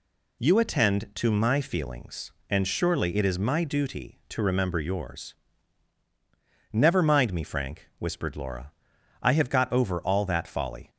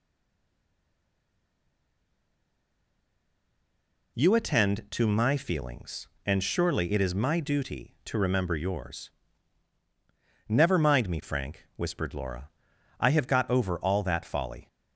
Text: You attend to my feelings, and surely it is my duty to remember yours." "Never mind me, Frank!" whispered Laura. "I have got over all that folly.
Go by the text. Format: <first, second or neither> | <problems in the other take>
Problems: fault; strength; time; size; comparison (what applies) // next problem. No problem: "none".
first | stays silent before the first word; strong; until 4.1 s; 4.1 s long